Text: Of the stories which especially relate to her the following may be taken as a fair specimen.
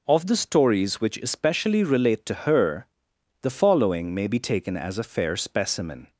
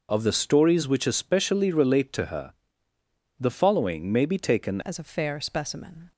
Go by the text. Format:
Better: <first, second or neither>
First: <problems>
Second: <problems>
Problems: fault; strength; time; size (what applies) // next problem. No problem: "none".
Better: first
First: pauses between "her" and "the"; noticeable; at 2.8 s; 0.56 s long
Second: pauses between "her" and "the"; noticeable; at 2.5 s; 0.86 s long // changes voice at "as"; from 4.8 s on; 1.3 s long